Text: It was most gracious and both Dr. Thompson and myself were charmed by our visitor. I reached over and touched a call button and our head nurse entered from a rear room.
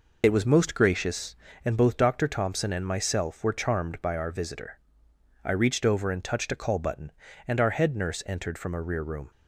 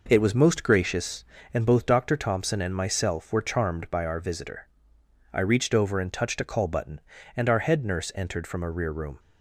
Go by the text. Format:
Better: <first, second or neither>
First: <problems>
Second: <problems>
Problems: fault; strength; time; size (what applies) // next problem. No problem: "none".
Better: second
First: loses the start of "It"; at 0.2 s; 70 ms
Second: none